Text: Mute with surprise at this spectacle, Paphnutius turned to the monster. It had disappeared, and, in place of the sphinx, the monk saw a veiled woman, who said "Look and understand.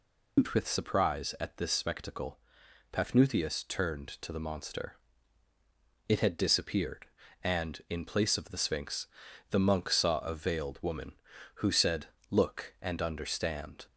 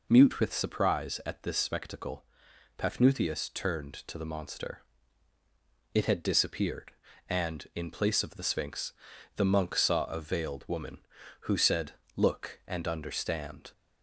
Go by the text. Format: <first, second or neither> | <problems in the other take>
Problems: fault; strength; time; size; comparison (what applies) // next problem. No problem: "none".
second | loses the start of "Mute"; at 0.3 s; 135 ms // pauses between "said" and "Look"; slight; at 12.0 s; 0.24 s long; slight in the second